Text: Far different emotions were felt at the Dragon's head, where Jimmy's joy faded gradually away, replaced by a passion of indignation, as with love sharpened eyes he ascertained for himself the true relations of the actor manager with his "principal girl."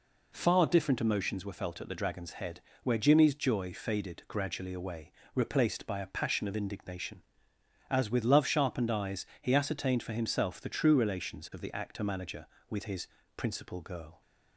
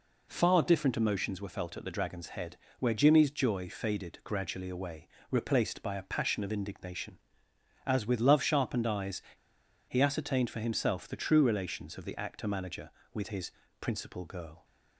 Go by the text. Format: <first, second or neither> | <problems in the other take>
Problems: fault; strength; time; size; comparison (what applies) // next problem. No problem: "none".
first | pauses between "eyes" and "he"; noticeable; at 9.2 s; 0.65 s long // pauses between "his" and "principal"; slight; at 13.5 s; 0.28 s long; slight in the first